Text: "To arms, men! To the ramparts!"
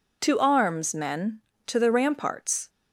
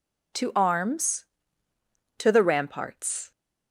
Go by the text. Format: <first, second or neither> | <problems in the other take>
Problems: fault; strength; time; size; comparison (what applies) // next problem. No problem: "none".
first | skips "men"; at 1.7 s